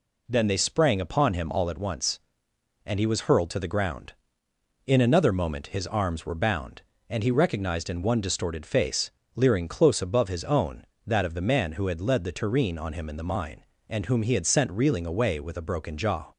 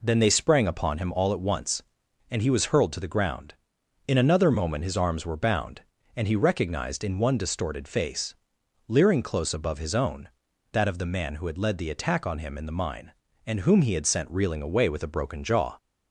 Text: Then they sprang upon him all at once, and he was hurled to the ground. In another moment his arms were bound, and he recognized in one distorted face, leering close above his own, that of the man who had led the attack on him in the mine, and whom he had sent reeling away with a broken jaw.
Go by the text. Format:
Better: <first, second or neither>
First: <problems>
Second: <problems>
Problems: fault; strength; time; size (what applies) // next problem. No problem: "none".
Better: second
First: says "tureen" for "attack"; at 12.3 s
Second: none